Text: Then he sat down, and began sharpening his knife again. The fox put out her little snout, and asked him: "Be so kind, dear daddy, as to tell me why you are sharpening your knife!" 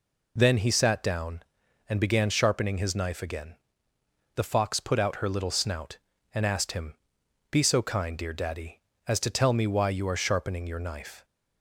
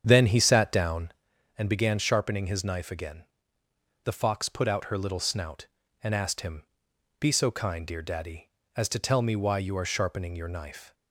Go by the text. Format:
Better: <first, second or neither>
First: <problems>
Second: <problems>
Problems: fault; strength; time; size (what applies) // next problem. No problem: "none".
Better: first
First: none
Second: starts louder than the rest; strong; until 1.3 s; 8 dB